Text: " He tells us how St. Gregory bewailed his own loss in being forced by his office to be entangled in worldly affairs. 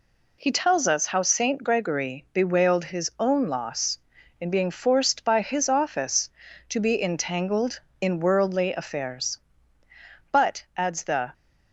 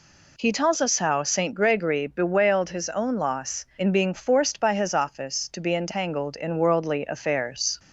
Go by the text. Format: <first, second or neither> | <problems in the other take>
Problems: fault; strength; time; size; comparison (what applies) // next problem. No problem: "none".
second | goes on to say "But adds the"; noticeable; from 10.3 s on; 1.0 s long